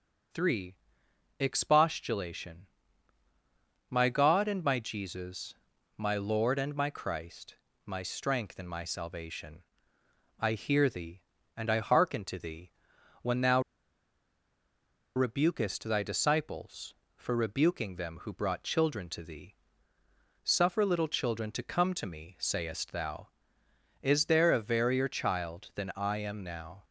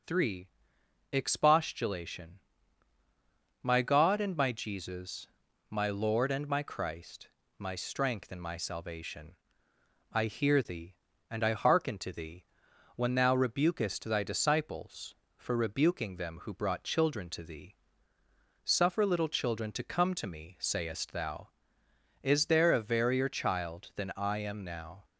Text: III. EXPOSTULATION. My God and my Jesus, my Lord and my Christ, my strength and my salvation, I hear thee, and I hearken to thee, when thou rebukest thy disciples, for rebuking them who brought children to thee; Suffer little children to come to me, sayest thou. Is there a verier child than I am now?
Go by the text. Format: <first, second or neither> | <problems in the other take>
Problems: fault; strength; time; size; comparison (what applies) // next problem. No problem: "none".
second | pauses between "thou" and "rebukest"; strong; at 13.6 s; 1.5 s long